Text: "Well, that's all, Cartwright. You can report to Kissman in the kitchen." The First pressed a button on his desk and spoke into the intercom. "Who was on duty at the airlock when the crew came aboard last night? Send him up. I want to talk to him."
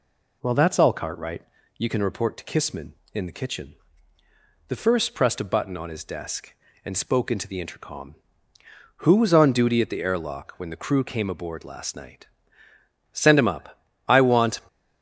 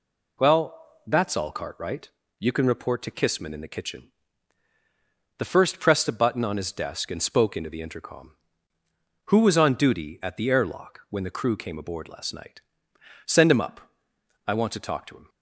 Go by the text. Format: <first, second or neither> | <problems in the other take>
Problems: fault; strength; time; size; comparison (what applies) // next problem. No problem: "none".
second | stops before "to talk to him"; at 14.6 s